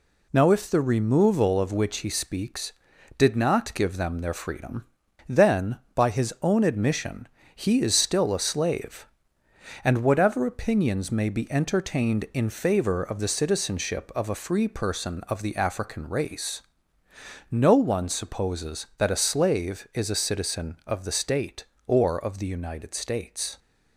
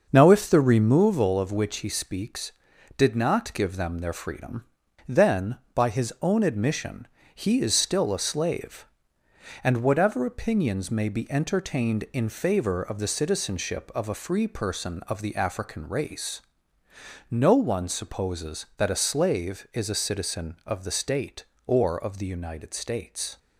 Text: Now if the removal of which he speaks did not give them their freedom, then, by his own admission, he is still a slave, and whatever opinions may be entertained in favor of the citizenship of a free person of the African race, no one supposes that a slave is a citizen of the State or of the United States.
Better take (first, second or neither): first